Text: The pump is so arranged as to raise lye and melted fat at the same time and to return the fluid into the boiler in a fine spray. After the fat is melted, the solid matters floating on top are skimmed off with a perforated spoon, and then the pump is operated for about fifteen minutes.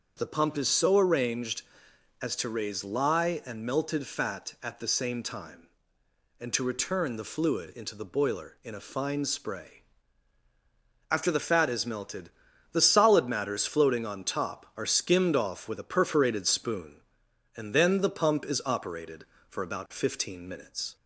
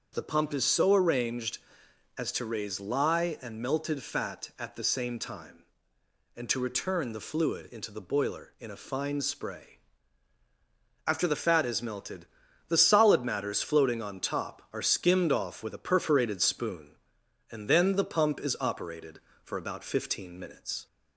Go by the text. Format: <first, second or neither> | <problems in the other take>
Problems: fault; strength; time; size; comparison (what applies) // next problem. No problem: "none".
neither | starts louder than the rest; the same in both